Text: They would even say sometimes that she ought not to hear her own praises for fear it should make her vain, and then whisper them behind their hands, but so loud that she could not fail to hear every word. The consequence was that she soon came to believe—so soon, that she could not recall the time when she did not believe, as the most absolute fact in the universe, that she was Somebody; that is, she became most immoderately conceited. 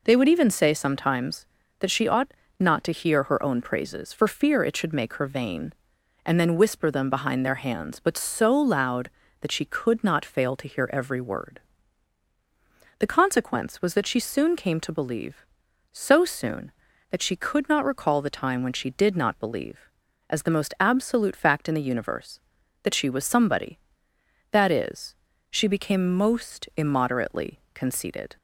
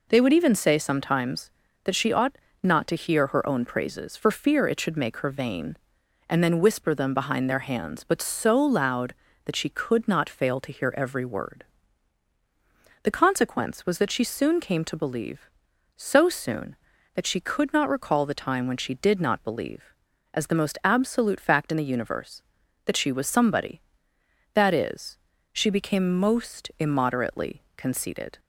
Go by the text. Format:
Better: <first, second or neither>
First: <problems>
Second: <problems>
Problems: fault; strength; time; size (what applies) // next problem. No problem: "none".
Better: neither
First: pauses between "ought" and "not"; slight; at 2.3 s; 0.26 s long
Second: pauses between "ought" and "not"; slight; at 2.3 s; 0.25 s long